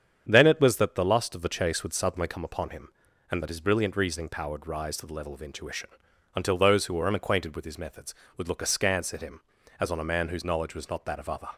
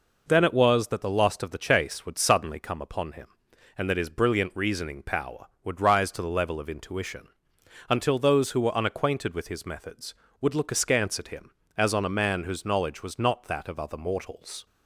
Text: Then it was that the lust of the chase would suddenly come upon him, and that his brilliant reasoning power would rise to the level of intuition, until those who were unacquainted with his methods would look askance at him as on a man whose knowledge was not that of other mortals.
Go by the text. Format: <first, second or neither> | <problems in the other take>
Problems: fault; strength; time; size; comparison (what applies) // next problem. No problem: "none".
second | starts louder than the rest; strong; until 1.3 s; 8 dB // stops before "mortals"; at 11.5 s